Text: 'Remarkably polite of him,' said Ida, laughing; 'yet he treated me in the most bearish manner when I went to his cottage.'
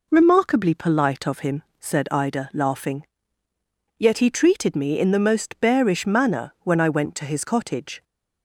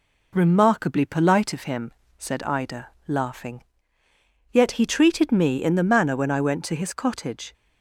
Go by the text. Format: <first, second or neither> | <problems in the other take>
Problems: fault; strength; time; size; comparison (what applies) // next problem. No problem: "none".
first | skips "most bearish"; at 5.8 s